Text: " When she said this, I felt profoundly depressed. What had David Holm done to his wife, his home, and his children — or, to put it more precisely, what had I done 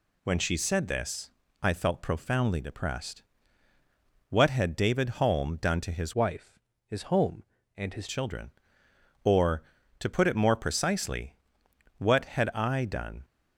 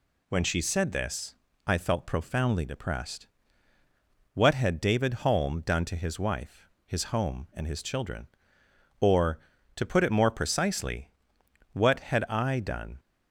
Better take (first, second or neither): second